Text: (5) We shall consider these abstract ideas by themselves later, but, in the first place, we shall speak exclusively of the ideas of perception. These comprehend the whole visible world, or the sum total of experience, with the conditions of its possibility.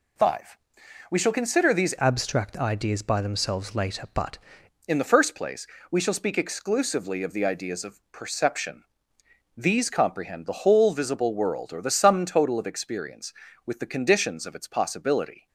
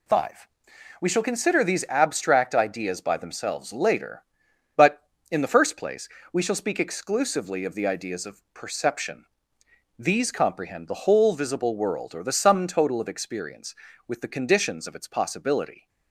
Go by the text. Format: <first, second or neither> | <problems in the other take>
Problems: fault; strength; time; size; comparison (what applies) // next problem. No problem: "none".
second | changes voice from "abstract" to "but"; from 1.9 to 4.3 s; 2.4 s long